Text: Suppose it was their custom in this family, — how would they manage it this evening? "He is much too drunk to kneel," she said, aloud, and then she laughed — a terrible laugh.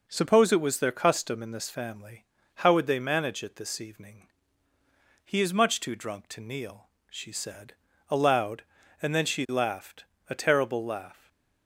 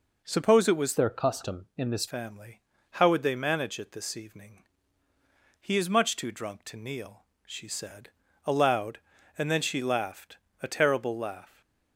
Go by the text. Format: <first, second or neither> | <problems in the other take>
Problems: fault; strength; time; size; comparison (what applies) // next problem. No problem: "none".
first | changes voice from "their" to "this"; from 0.9 to 2.0 s; 1.1 s long // stays silent after the last word; slight; from 11.4 s on; 0.5 s long; slight in the first